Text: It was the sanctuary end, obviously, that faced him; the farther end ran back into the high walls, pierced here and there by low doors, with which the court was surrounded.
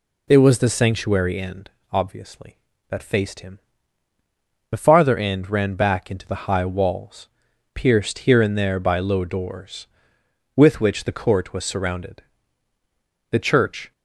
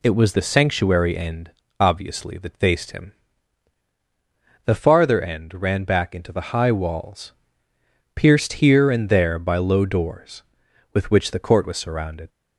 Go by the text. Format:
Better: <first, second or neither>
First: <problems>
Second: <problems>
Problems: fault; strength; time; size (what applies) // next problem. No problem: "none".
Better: second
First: goes on to say "The church"; noticeable; from 13.2 s on; 0.62 s long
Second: none